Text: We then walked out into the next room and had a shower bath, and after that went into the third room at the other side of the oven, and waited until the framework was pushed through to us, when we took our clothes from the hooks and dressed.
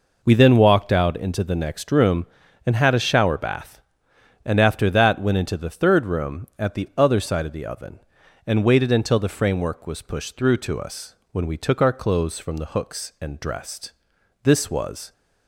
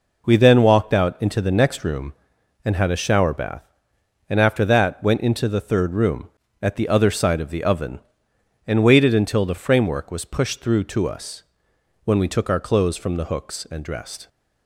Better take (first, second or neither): second